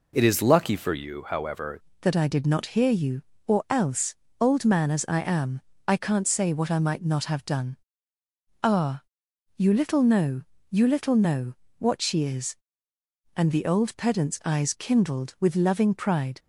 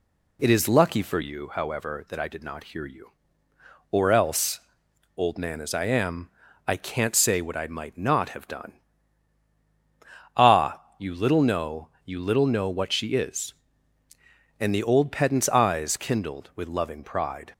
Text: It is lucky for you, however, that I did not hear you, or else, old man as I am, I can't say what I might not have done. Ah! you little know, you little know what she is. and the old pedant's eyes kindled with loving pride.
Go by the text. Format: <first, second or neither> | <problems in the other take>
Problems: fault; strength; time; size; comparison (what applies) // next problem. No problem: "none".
second | changes voice at "that"; from 2.0 s on; 14.3 s long // pauses between "know" and "what"; slight; at 11.5 s; 0.24 s long